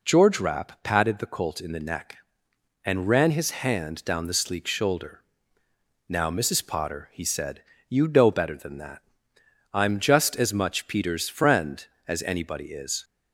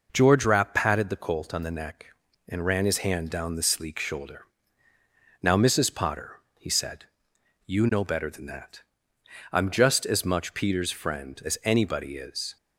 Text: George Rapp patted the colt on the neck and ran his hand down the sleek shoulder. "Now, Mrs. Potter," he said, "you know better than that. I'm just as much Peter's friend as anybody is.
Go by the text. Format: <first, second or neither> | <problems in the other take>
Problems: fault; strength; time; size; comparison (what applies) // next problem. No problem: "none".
second | says "in" for "on"; at 1.6 s